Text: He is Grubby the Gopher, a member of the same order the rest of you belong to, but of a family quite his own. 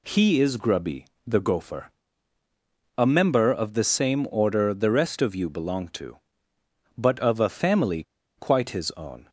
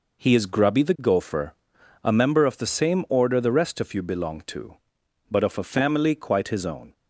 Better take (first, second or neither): second